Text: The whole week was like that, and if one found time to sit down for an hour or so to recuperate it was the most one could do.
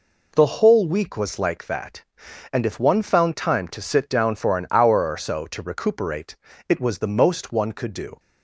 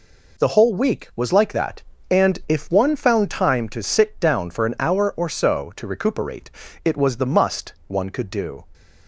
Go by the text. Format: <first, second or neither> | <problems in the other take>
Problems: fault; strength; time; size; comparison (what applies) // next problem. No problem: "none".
first | pauses between "recuperate" and "it"; slight; at 6.4 s; 0.34 s long; slight in the first // says "must" for "most"; at 7.2 s